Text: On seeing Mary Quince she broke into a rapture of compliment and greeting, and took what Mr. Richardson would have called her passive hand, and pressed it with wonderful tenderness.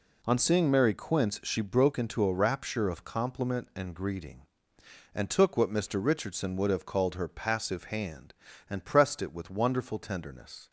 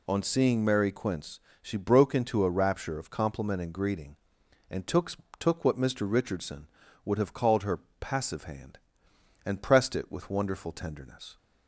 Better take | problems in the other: first | pauses between "Quince" and "she"; slight; at 1.3 s; 0.24 s long // says "took" twice; at 5.3 s // pauses between "her" and "passive"; slight; at 7.7 s; 0.22 s long

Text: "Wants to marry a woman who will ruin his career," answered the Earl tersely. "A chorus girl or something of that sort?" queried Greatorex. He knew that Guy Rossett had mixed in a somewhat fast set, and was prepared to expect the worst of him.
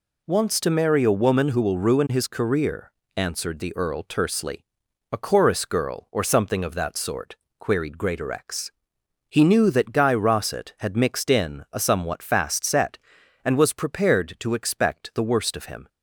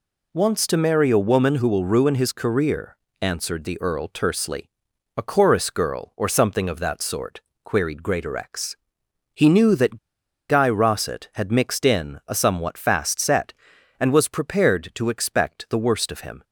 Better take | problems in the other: first | pauses between "that" and "Guy"; noticeable; at 9.9 s; 0.51 s long

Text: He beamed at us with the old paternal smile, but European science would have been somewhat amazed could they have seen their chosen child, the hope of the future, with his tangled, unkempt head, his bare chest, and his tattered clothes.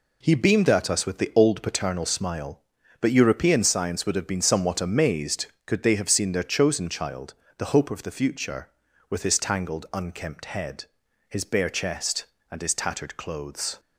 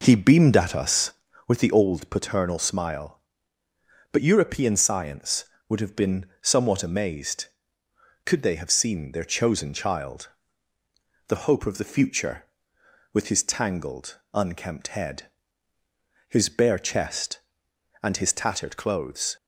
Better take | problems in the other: first | starts louder than the rest; noticeable; until 1.7 s; 4.5 dB // pauses between "been" and "somewhat"; slight; at 6.2 s; 0.16 s long

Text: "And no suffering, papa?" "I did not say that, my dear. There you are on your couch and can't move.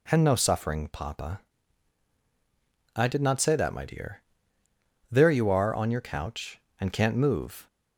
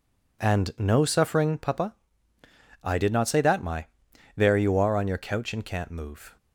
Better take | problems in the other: first | skips "dear"; at 4.1 s

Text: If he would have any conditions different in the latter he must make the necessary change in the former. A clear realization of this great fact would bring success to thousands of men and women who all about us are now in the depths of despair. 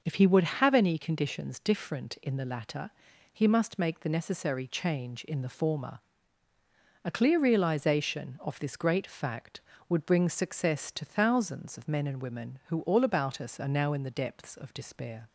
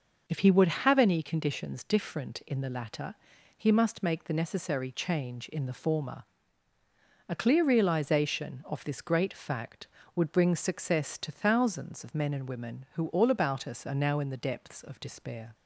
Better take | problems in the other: neither | pauses between "latter" and "he"; the same in both

